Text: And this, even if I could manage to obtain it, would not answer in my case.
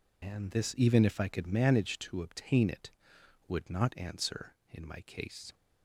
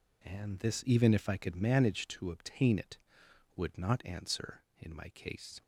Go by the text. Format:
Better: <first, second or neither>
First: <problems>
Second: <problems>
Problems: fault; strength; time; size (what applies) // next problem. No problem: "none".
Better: second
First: loses the start of "And"; at 0.2 s; 60 ms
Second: none